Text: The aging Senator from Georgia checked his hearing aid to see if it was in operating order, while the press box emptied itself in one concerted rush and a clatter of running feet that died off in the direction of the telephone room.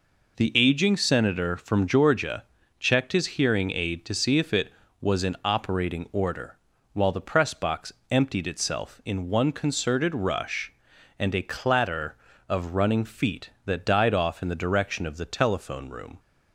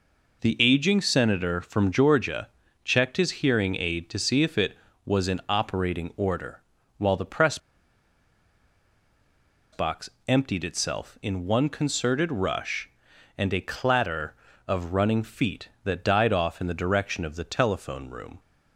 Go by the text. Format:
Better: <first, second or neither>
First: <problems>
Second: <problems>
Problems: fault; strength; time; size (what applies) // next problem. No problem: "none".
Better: first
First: pauses between "Georgia" and "checked"; at 2.4 s; 0.38 s long // pauses between "box" and "emptied"; slight; at 7.9 s; 0.18 s long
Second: pauses between "Georgia" and "checked"; at 2.4 s; 0.38 s long // pauses between "press" and "box"; strong; at 7.5 s; 2.1 s long // pauses between "box" and "emptied"; slight; at 10.0 s; 0.18 s long